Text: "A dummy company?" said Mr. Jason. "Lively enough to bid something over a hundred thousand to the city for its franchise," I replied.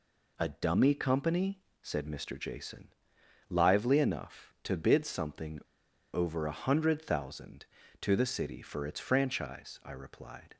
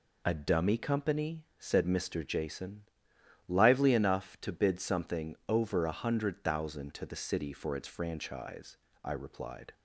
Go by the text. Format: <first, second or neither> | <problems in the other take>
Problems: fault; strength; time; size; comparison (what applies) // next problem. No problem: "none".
second | pauses between "something" and "over"; noticeable; at 5.6 s; 0.52 s long